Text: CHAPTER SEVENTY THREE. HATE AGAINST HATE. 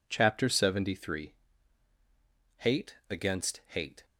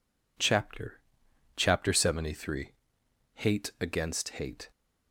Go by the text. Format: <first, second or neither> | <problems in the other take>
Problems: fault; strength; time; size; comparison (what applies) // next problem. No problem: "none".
first | says "CHAPTER" twice; at 1.5 s